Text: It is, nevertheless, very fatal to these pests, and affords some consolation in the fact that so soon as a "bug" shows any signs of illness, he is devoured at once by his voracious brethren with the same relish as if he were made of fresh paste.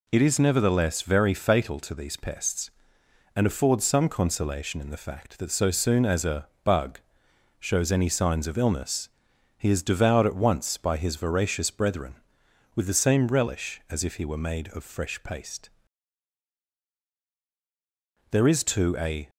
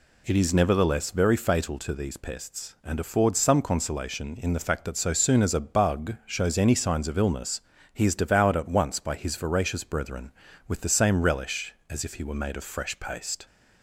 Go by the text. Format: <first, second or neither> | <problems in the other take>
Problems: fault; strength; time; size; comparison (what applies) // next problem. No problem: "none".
second | pauses between "a" and "bug"; slight; at 6.4 s; 0.16 s long // pauses between "bug" and "shows"; noticeable; at 7.0 s; 0.58 s long // goes on to say "There is too a"; noticeable; from 18.2 s on; 1.0 s long